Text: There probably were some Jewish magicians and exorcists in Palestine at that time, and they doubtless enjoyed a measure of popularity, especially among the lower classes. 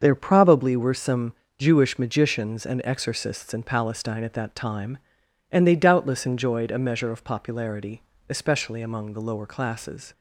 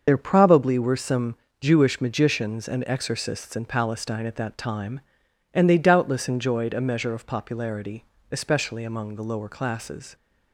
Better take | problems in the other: first | loses the start of "There"; at 0.0 s; 40 ms // starts louder than the rest; until 1.0 s; 6.5 dB; also in the first // pauses between "some" and "Jewish"; slight; at 1.3 s; 0.26 s long; slight in the first

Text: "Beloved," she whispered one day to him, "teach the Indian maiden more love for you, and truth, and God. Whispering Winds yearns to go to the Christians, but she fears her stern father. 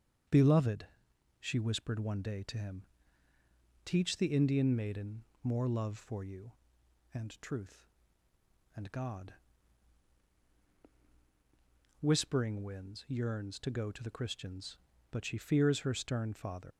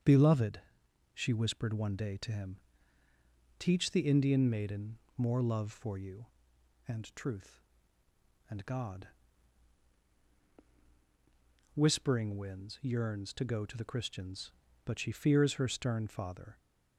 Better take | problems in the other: second | starts louder than the rest; strong; until 1.8 s; 7.5 dB; strong in the second // pauses between "maiden" and "more"; slight; at 5.2 s; 0.18 s long; slight in the second // leaves "father" unfinished; at 16.7 s; 125 ms

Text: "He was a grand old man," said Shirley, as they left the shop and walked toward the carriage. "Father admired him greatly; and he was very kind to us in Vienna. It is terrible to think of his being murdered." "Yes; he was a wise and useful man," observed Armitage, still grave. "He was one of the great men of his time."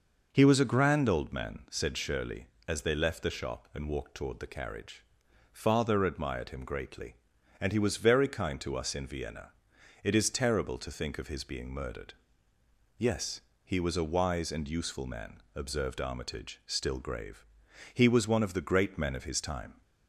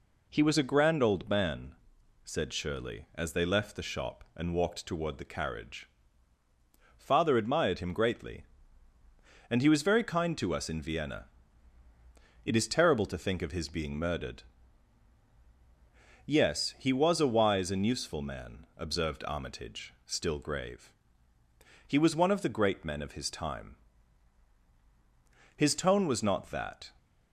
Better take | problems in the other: first | goes on to say "His tone was not that"; from 25.5 s on; 1.3 s long

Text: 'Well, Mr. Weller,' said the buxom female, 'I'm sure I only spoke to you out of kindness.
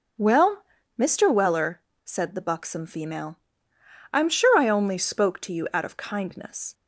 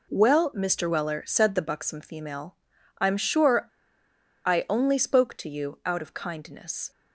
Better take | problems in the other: first | pauses between "sure" and "I"; noticeable; at 3.6 s; 0.78 s long

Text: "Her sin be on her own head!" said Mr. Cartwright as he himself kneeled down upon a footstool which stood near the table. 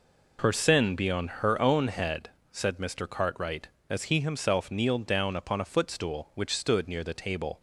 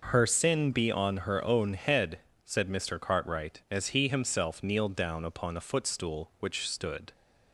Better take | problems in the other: first | stops before "near the table"; at 7.1 s

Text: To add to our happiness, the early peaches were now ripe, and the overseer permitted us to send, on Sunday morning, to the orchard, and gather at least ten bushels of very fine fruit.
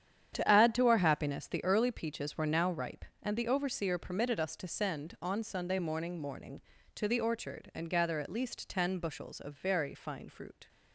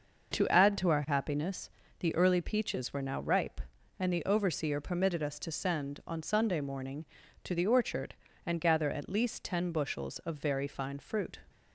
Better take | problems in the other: second | starts louder than the rest; strong; until 1.3 s; 9 dB // says "morning" twice; at 6.1 s

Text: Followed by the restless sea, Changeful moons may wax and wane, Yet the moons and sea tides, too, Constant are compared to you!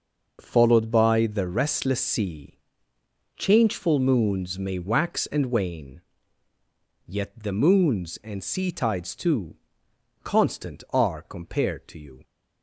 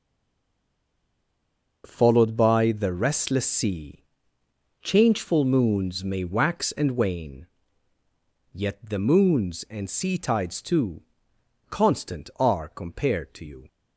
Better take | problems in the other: first | stays silent before the first word; noticeable; until 1.8 s; 1.8 s long

